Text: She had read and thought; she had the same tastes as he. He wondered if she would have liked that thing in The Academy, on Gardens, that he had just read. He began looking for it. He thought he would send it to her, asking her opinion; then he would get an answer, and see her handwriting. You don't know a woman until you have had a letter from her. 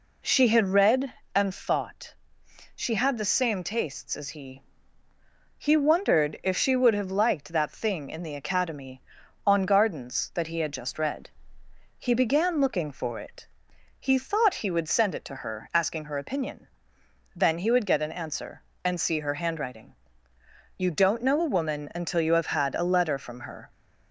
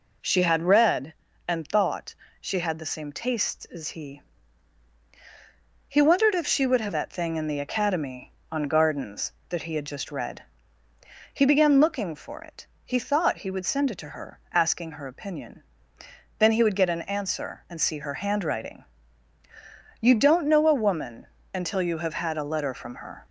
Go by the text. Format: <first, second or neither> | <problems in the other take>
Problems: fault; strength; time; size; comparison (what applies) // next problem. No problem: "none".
first | skips "liked"; at 6.9 s // pauses between "woman" and "until"; slight; at 21.2 s; 0.30 s long